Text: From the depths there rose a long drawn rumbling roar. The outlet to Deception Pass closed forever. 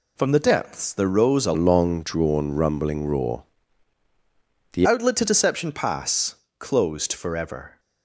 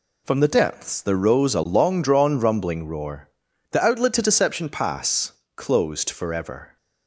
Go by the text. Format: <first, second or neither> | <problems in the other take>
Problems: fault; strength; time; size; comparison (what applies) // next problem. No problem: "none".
second | changes voice from "long" to "The"; from 1.5 to 4.8 s; 3.3 s long // pauses between "Pass" and "closed"; slight; at 6.3 s; 0.24 s long; slight in the second